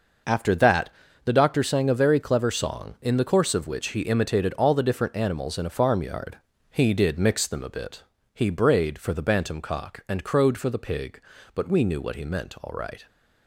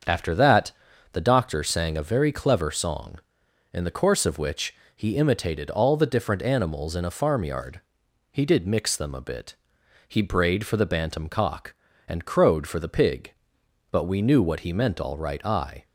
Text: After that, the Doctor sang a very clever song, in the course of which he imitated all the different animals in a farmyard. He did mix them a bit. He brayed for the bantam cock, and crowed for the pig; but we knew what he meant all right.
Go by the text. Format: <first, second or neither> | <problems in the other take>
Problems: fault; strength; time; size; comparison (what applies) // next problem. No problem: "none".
first | starts louder than the rest; until 1.4 s; 7 dB // pauses between "which" and "he"; slight; at 4.7 s; 0.22 s long // goes on to say "I"; slight; from 15.4 s on; 0.40 s long